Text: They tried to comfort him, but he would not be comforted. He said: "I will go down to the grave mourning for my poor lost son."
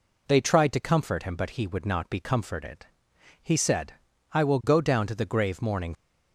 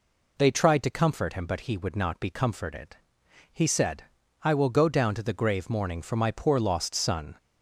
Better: second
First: stops before "for my poor lost son"; at 5.9 s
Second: none

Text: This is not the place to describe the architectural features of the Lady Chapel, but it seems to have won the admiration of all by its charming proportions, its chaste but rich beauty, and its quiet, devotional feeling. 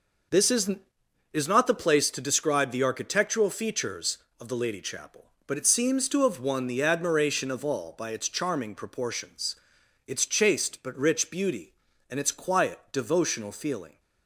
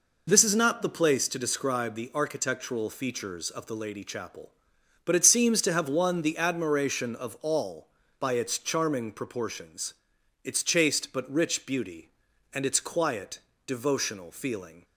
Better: second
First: says "is" twice; at 1.3 s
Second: none

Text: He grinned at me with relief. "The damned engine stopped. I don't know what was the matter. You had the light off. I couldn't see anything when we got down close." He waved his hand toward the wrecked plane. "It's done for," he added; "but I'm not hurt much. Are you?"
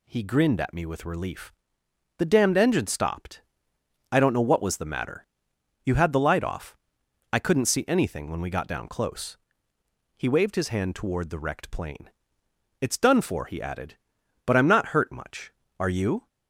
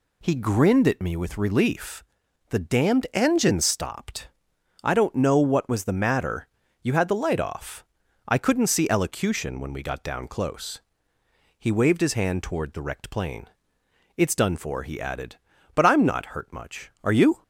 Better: first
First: none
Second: says "elocution" for "anything"; at 8.9 s

